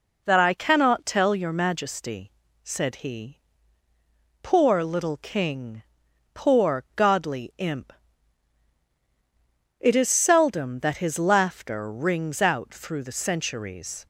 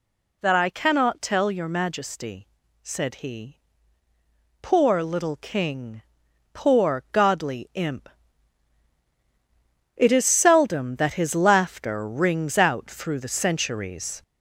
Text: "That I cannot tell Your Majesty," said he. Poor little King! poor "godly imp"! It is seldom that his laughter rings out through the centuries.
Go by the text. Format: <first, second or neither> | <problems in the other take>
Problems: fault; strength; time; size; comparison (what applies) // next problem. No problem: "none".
first | gets louder; noticeable; throughout; 4 dB